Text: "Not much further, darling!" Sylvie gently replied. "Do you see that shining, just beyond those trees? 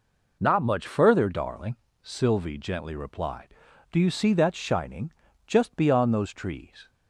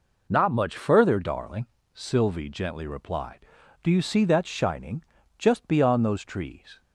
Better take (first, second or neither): neither